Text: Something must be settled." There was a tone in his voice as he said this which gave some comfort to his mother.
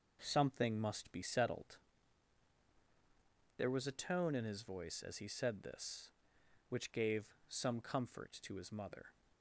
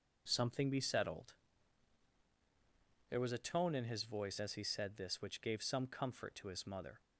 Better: first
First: none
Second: skips "must"; at 0.7 s

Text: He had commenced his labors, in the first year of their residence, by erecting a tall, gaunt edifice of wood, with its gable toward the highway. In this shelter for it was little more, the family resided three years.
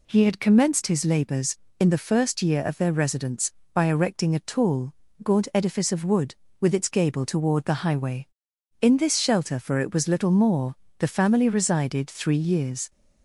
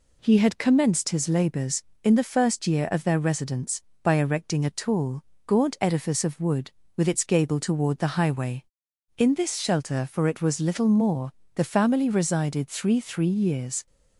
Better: first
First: none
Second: says "three" twice; at 12.9 s

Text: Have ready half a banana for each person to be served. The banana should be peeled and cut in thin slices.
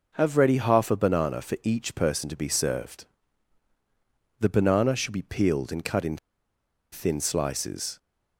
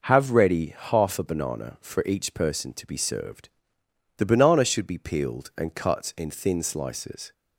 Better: second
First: pauses between "in" and "thin"; noticeable; at 6.1 s; 0.75 s long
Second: none

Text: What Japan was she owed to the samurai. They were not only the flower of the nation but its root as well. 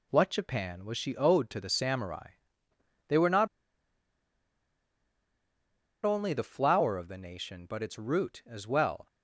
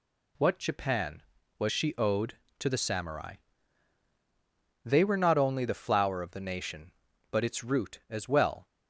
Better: second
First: pauses between "not" and "only"; strong; at 3.4 s; 2.5 s long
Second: none

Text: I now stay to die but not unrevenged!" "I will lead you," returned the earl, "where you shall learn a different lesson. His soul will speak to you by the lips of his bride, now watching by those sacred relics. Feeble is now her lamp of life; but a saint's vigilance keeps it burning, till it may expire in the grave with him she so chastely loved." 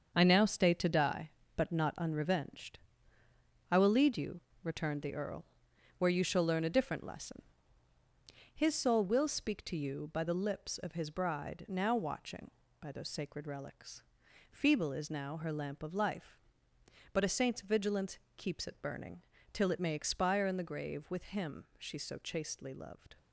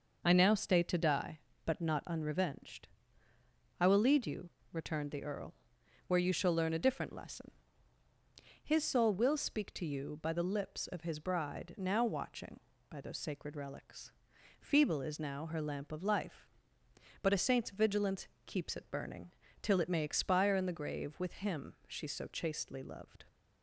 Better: second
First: gets quieter; strong; throughout; 8 dB // pauses between "vigilance" and "keeps"; slight; at 18.1 s; 0.18 s long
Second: pauses between "vigilance" and "keeps"; slight; at 18.2 s; 0.18 s long

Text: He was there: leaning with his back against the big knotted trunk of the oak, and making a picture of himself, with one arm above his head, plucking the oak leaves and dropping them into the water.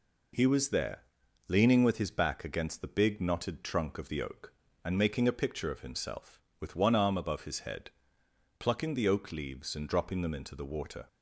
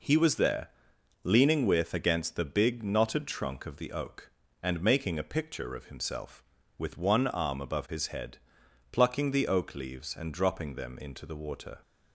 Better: first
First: none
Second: skips "his back"; at 1.9 s

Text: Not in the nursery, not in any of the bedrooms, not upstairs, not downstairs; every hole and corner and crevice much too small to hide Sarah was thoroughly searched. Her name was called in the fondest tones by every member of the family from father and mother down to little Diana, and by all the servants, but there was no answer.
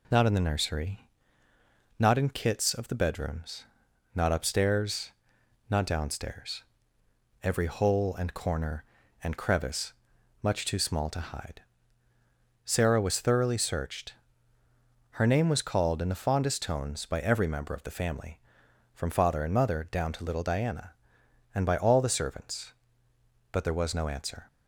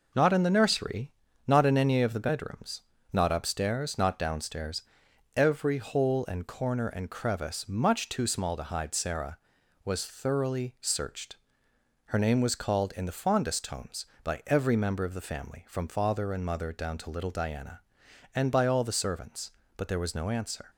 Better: second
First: says "kits" for "any"; at 2.2 s // pauses between "crevice" and "much"; noticeable; at 9.9 s; 0.50 s long // pauses between "hide" and "Sarah"; at 11.6 s; 1.0 s long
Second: none

